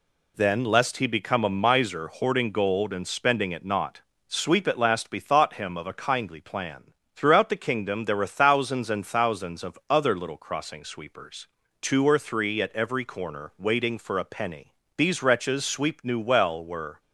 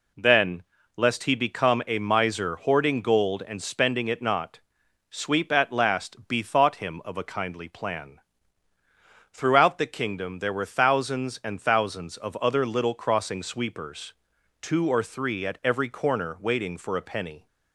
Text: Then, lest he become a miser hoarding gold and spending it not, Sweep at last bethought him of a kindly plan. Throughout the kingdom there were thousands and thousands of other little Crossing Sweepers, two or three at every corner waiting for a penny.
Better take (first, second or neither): second